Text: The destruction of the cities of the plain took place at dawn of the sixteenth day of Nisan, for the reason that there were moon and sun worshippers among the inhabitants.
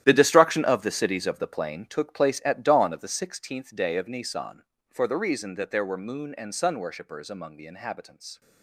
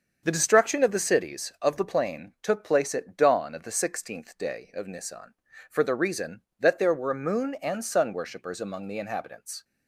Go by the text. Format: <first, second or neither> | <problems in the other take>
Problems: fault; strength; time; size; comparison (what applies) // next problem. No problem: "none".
second | gets quieter; strong; throughout; 14 dB // starts louder than the rest; strong; until 1.0 s; 12 dB; also in the second